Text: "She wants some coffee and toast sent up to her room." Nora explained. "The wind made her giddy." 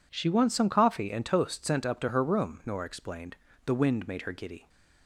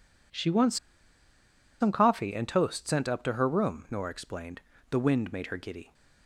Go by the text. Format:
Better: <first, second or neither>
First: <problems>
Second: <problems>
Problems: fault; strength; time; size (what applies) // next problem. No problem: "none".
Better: first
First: none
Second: pauses between "wants" and "some"; at 0.7 s; 1.0 s long